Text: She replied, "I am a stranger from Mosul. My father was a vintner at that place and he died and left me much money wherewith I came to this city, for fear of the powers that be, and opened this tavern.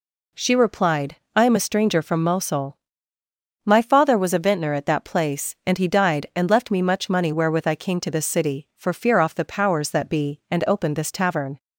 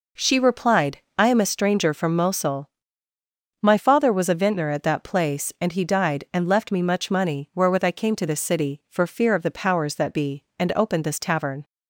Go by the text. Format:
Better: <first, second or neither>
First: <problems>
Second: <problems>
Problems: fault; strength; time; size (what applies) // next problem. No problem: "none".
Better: second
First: says "off" for "of"; at 9.1 s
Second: none